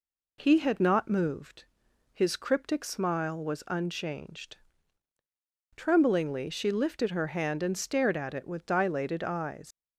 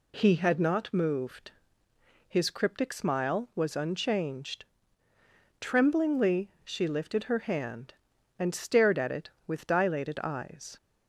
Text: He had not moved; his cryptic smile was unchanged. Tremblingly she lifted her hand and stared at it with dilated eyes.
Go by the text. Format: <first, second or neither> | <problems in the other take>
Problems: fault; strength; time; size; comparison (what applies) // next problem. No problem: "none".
second | leaves "eyes" unfinished; at 9.7 s; 110 ms